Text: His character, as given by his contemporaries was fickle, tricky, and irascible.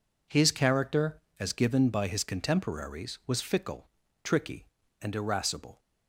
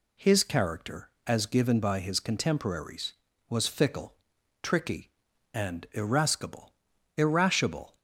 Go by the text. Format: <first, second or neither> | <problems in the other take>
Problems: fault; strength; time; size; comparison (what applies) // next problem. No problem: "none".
first | says "irascible" twice; at 7.1 s